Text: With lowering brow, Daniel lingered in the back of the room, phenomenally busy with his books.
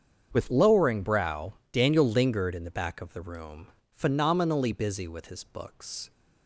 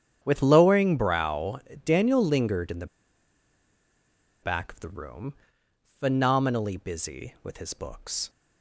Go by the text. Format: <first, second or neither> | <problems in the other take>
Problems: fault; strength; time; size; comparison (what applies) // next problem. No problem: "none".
first | starts louder than the rest; strong; until 1.2 s; 8.5 dB; strong in the first // pauses between "the" and "back"; strong; at 2.8 s; 1.5 s long